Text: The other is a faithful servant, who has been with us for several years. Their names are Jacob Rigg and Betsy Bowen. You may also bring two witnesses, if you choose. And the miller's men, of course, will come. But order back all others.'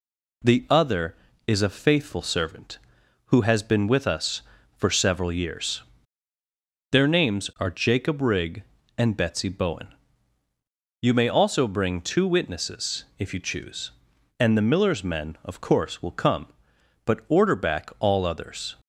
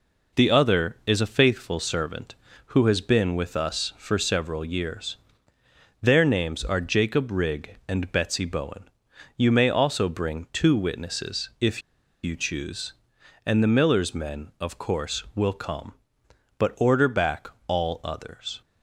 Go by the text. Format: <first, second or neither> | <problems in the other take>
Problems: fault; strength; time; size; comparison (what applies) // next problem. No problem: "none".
first | pauses between "if" and "you"; at 11.8 s; 0.43 s long // pauses between "back" and "all"; slight; at 17.4 s; 0.18 s long